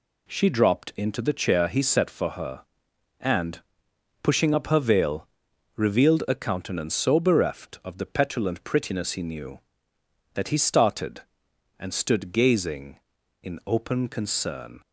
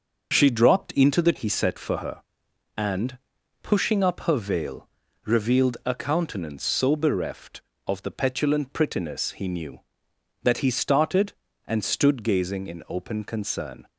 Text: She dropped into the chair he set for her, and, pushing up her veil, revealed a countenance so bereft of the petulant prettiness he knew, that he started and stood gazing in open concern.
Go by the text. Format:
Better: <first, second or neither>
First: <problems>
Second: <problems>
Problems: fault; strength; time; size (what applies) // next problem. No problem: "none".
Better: first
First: none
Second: starts louder than the rest; noticeable; until 1.3 s; 6 dB // skips "chair"; at 1.3 s